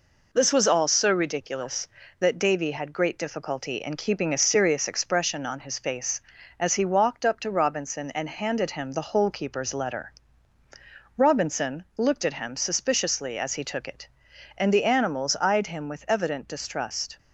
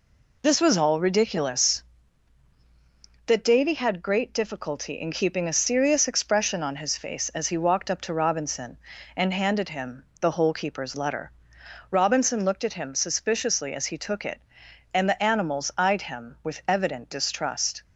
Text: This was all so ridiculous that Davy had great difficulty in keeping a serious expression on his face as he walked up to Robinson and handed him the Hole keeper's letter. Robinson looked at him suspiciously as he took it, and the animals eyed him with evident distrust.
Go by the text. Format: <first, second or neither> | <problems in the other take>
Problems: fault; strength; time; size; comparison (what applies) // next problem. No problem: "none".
first | skips "so"; at 1.0 s // pauses between "him" and "the"; slight; at 10.0 s; 0.16 s long